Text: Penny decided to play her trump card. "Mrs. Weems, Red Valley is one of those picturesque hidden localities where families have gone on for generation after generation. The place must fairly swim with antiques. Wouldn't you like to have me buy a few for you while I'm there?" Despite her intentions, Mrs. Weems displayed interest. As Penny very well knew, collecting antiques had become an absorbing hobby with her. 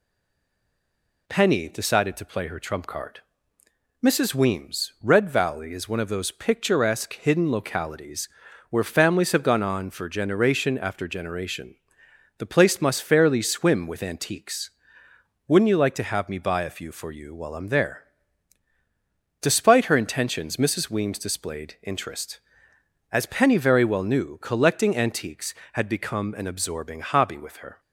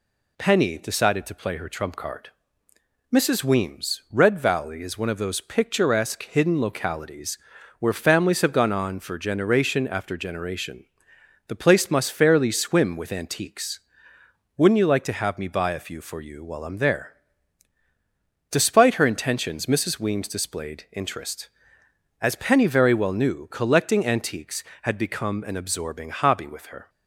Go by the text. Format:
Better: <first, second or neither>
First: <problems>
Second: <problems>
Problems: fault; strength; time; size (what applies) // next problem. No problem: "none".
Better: second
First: stays silent before the first word; noticeable; until 1.2 s; 1.2 s long // pauses between "localities" and "where"; at 8.2 s; 0.42 s long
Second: pauses between "localities" and "where"; at 7.3 s; 0.42 s long